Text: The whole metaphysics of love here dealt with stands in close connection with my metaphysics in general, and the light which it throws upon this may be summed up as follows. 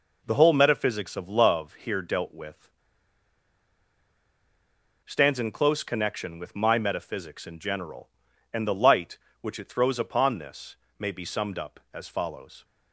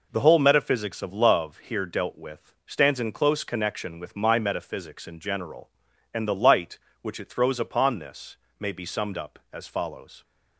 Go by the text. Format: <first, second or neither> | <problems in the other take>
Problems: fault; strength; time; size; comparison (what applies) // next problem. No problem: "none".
second | pauses between "with" and "stands"; strong; at 2.6 s; 2.3 s long // pauses between "this" and "may"; slight; at 10.7 s; 0.24 s long; slight in the second